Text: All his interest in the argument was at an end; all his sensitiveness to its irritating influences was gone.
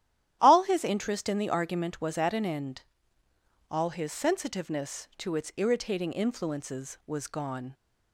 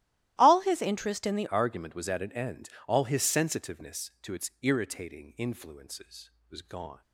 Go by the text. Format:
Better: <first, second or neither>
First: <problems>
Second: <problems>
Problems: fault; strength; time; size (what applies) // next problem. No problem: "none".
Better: first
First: starts louder than the rest; strong; until 1.4 s; 11.5 dB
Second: starts louder than the rest; strong; until 1.3 s; 15 dB // changes voice at "argument"; from 1.4 s on; 5.6 s long